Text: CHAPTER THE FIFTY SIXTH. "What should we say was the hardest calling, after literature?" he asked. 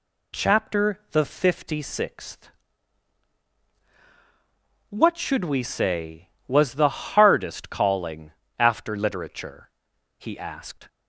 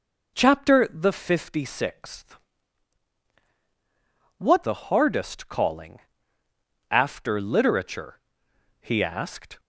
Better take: first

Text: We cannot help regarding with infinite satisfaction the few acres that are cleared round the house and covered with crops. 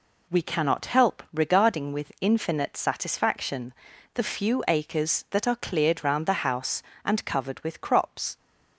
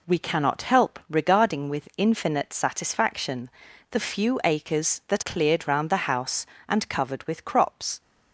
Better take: first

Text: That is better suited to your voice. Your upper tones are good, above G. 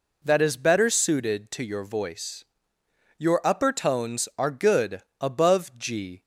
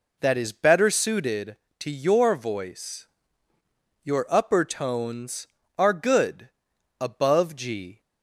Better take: neither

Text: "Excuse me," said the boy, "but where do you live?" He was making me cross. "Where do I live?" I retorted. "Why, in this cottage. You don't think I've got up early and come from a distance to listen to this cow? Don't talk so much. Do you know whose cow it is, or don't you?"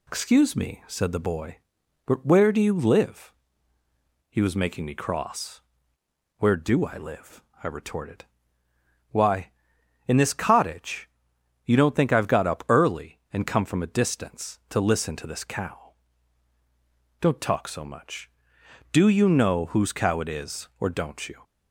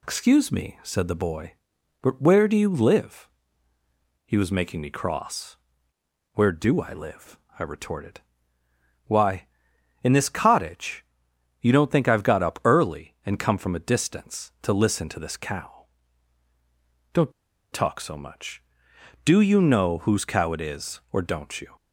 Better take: first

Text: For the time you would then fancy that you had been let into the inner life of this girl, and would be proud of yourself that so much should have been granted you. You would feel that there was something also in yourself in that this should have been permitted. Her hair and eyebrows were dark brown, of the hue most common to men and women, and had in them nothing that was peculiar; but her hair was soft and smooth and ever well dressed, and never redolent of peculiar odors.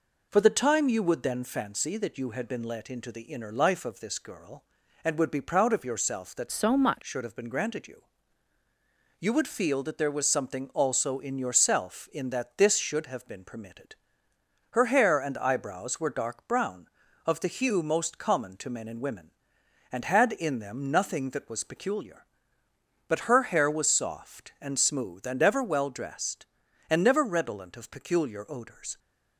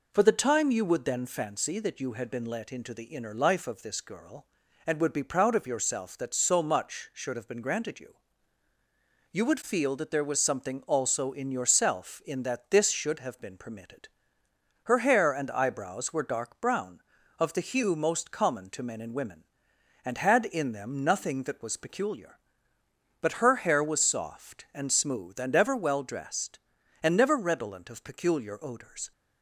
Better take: second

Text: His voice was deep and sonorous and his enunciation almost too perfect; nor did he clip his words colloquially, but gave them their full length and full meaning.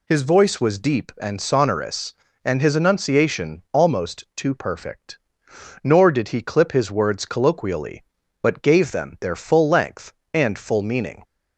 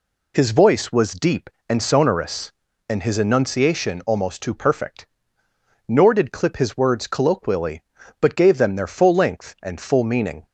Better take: first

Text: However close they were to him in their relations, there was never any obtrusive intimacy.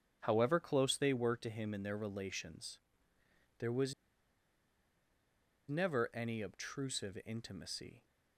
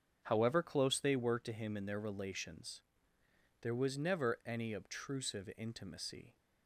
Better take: second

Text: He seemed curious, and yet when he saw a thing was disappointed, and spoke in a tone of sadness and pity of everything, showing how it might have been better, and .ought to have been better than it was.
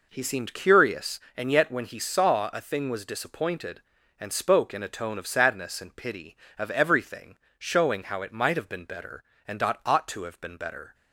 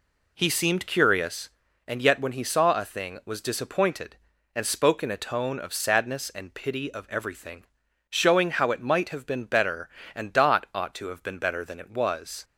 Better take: second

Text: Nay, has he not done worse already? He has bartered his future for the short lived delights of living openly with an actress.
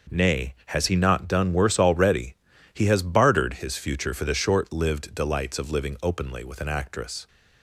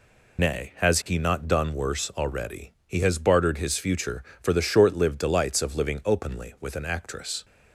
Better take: first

